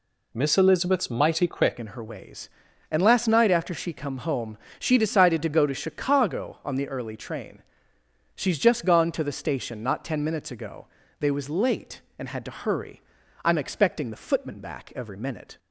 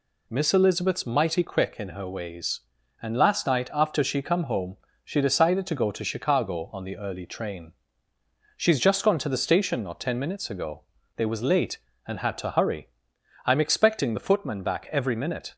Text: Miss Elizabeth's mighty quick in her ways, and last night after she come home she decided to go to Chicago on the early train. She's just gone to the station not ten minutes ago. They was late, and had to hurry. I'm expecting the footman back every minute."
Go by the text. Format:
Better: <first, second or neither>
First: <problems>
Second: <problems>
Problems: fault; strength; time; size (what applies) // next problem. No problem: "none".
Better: second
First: changes voice at "in"; from 1.7 s on; 13.8 s long // pauses between "home" and "she"; slight; at 4.5 s; 0.22 s long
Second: pauses between "home" and "she"; slight; at 4.7 s; 0.30 s long